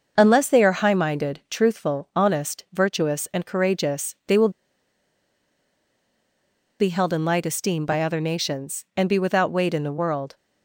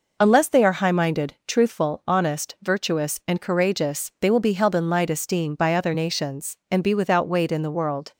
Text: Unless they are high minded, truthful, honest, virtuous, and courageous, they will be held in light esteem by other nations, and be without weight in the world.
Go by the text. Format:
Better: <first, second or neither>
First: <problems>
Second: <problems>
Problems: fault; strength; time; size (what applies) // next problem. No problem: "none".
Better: second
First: starts louder than the rest; until 1.1 s; 6 dB // pauses between "will" and "be"; strong; at 4.4 s; 2.3 s long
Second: none